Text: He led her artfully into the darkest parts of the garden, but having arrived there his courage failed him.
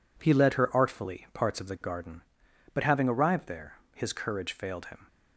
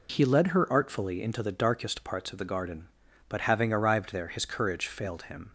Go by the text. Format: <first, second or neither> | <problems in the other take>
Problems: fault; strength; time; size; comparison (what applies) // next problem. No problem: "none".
second | skips "into the darkest"; at 1.2 s // pauses between "there" and "his"; slight; at 3.7 s; 0.18 s long